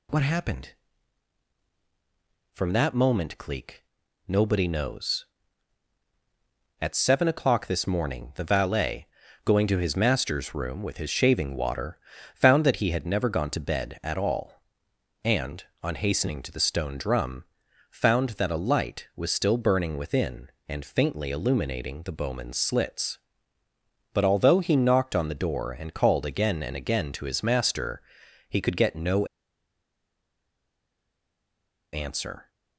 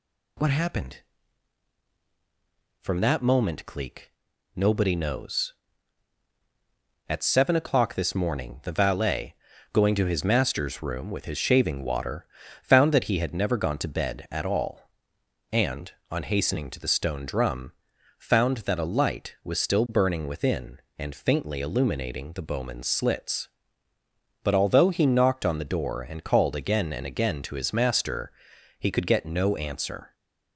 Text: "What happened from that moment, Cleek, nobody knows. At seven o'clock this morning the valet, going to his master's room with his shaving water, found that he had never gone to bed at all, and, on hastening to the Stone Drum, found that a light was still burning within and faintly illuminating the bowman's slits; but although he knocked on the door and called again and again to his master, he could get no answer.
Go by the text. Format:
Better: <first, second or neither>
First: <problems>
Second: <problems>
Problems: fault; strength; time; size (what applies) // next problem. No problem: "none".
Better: second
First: pauses between "no" and "answer"; strong; at 29.2 s; 2.6 s long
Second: none